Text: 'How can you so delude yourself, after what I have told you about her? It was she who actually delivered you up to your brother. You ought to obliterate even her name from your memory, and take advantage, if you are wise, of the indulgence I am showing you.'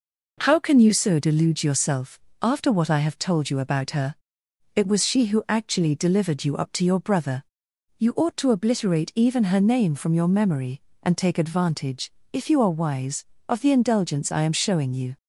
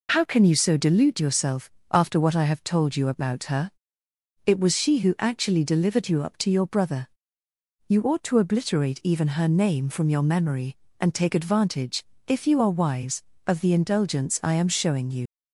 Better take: first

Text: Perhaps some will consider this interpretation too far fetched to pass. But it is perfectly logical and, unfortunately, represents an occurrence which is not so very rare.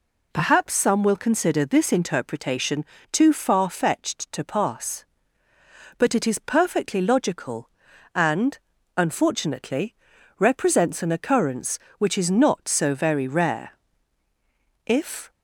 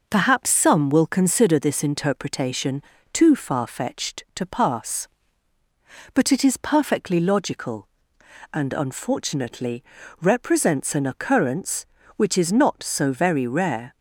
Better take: second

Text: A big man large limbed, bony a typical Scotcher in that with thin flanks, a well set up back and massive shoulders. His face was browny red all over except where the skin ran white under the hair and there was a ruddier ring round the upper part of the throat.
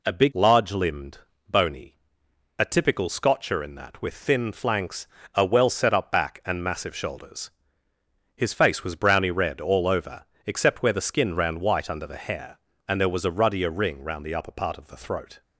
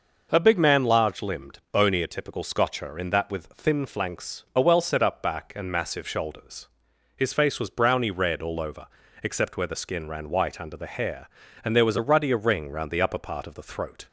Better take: second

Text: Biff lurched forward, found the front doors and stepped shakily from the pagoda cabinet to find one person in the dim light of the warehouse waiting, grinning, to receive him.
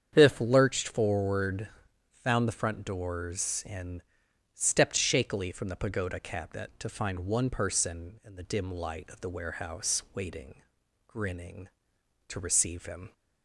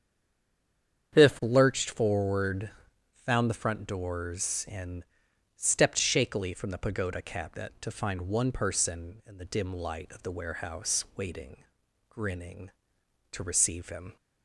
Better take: first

